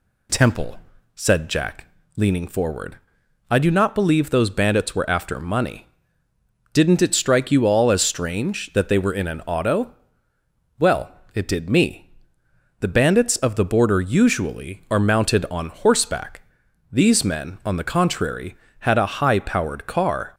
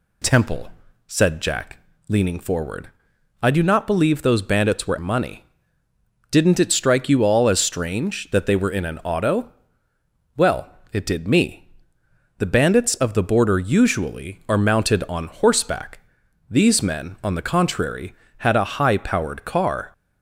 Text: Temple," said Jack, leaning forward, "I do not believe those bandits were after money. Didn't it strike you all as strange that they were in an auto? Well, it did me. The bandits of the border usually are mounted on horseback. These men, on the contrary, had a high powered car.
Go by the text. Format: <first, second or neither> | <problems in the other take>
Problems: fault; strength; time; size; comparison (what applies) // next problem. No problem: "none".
first | skips "after"; at 4.9 s